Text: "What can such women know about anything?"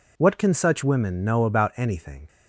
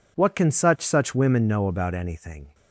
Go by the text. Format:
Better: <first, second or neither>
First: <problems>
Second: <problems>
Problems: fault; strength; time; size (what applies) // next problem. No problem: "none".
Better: first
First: none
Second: says "such" twice; at 0.8 s